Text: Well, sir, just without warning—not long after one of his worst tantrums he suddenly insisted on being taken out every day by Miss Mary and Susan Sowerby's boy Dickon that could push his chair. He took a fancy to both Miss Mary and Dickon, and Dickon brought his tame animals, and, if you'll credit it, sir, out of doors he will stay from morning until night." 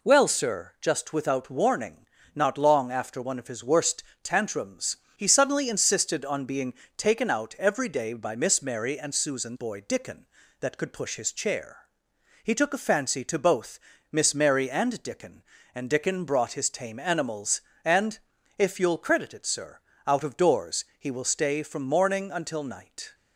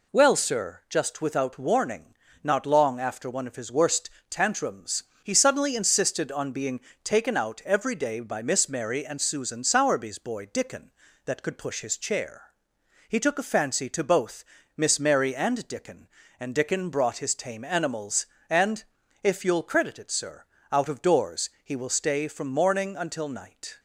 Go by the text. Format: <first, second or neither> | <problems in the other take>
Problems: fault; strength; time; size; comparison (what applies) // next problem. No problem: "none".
second | pauses between "worst" and "tantrums"; slight; at 4.0 s; 0.20 s long; slight in the second // pauses between "tantrums" and "he"; slight; at 4.9 s; 0.22 s long; slight in the second // pauses between "being" and "taken"; slight; at 6.7 s; 0.24 s long; slight in the second // skips "Sowerby's"; at 9.5 s // pauses between "both" and "Miss"; slight; at 13.7 s; 0.32 s long; slight in the second // pauses between "doors" and "he"; slight; at 20.8 s; 0.16 s long; slight in the second